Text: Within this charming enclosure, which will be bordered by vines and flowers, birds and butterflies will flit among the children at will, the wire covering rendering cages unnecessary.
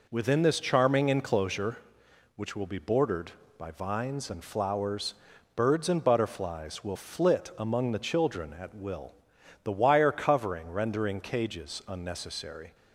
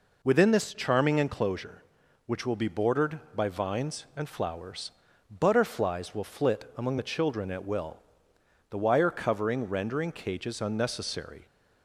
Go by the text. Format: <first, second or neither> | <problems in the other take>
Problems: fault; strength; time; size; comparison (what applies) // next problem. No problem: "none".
first | skips "birds and"; at 5.1 s